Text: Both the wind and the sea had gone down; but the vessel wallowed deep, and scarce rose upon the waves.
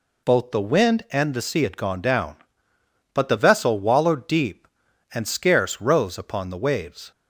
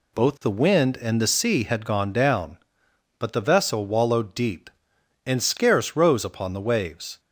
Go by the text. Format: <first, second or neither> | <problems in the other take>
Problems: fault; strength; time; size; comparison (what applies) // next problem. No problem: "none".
neither | none